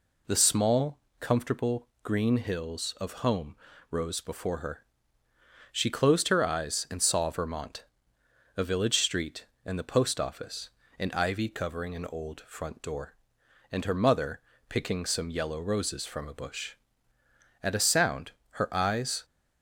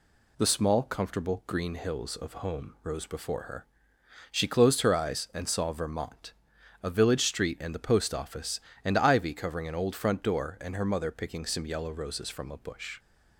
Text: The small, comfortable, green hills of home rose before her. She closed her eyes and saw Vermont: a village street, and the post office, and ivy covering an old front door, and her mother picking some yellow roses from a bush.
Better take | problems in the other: second | pauses between "home" and "rose"; slight; at 3.5 s; 0.34 s long // pauses between "mother" and "picking"; slight; at 14.3 s; 0.30 s long // goes on to say "At a sound her eyes"; from 17.6 s on; 1.6 s long

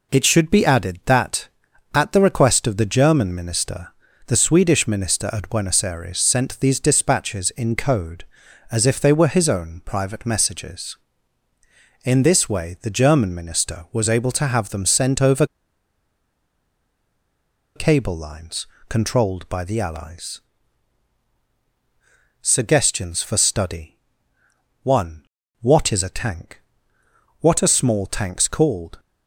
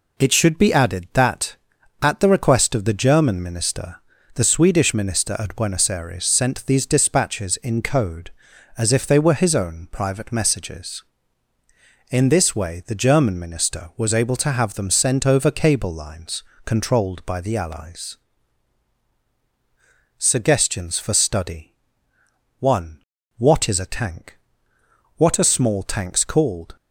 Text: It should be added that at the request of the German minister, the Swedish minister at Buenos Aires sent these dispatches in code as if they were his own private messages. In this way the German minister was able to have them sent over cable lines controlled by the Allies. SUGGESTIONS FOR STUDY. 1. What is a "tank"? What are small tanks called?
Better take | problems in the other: second | pauses between "over" and "cable"; strong; at 15.4 s; 2.3 s long // pauses between "lines" and "controlled"; slight; at 18.6 s; 0.22 s long; slight in the second

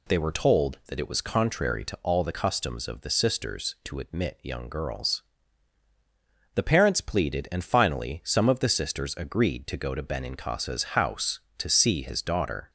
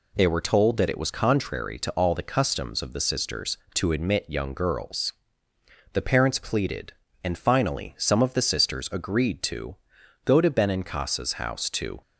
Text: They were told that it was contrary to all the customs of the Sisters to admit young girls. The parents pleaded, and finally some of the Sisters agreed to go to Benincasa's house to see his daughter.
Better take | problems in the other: first | pauses between "to" and "go"; noticeable; at 9.7 s; 0.50 s long // stops before "see his daughter"; at 12.0 s

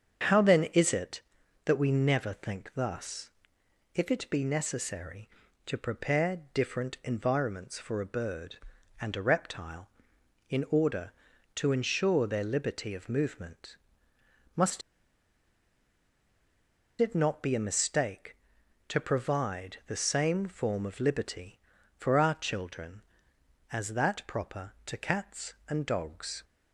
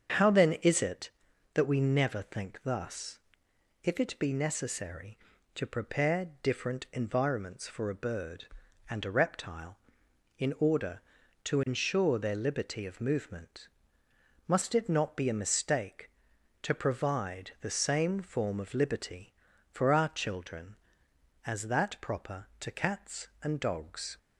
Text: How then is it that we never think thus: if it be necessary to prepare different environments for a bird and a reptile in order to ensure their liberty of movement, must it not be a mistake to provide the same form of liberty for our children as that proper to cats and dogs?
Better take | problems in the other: second | starts louder than the rest; strong; until 1.7 s; 7 dB; strong in the second // pauses between "must" and "it"; strong; at 14.8 s; 2.2 s long

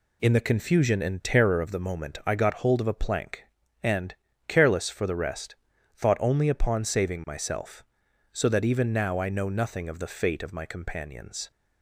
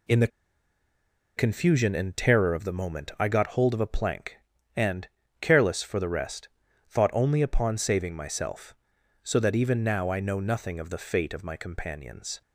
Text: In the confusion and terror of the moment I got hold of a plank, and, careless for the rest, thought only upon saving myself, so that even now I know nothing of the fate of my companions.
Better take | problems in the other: first | pauses between "the" and "confusion"; at 0.2 s; 1.0 s long

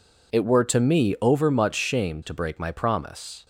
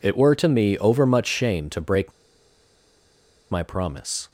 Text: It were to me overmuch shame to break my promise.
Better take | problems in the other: first | pauses between "break" and "my"; strong; at 2.1 s; 1.3 s long

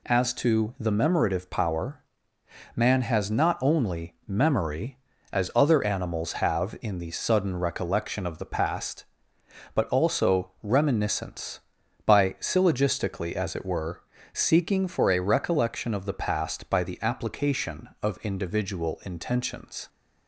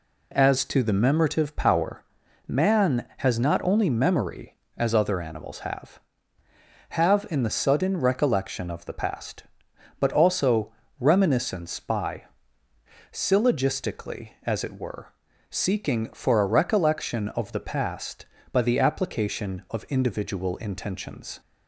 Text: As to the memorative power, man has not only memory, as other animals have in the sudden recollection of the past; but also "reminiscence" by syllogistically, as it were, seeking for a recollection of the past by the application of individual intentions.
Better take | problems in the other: first | says "have" twice; at 6.9 s // pauses between "also" and "reminiscence"; slight; at 10.7 s; 0.26 s long // pauses between "by" and "syllogistically"; noticeable; at 12.2 s; 0.88 s long

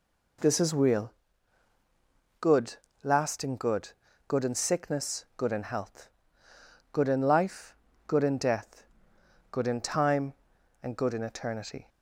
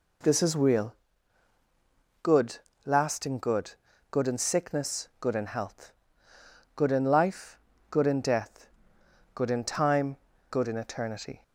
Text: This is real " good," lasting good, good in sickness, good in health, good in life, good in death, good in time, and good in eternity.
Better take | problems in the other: first | skips "and"; at 10.3 s

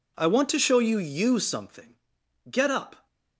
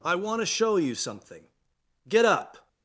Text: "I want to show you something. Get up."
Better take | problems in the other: second | says "you" twice; at 0.9 s

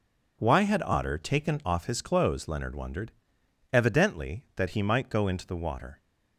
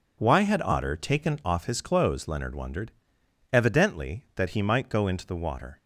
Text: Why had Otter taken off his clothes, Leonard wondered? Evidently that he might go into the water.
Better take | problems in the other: neither | none

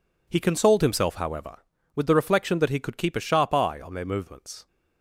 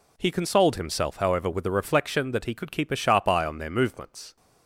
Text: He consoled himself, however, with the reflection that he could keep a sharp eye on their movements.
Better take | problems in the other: neither | none

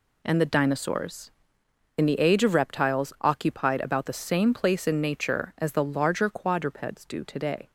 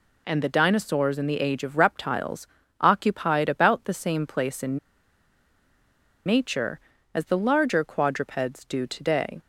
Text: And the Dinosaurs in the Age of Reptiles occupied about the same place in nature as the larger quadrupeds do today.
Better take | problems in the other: first | pauses between "Reptiles" and "occupied"; slight; at 2.4 s; 0.32 s long // pauses between "in" and "nature"; strong; at 4.7 s; 1.4 s long

